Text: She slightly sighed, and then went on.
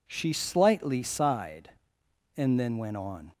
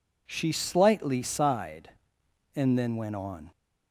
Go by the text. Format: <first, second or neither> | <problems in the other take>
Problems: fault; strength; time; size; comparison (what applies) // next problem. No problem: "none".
neither | none